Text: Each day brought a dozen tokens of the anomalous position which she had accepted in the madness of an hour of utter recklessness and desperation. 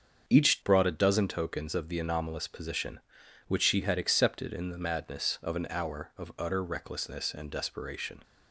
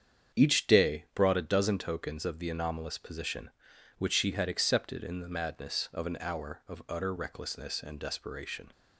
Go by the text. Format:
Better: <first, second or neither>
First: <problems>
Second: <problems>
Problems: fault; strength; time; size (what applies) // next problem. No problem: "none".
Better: second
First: starts louder than the rest; until 1.3 s; 7 dB // skips "day"; at 0.6 s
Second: starts louder than the rest; strong; until 1.4 s; 8 dB